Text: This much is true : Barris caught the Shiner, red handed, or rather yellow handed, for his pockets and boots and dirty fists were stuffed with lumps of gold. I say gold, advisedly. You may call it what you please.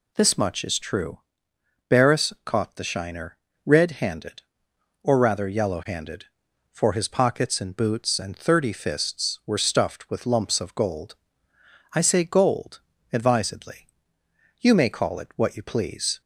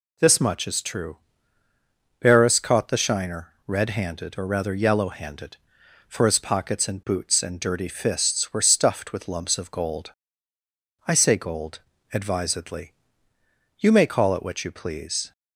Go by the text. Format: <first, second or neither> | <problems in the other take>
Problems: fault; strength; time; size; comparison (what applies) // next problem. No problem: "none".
second | says "thirty" for "dirty"; at 8.3 s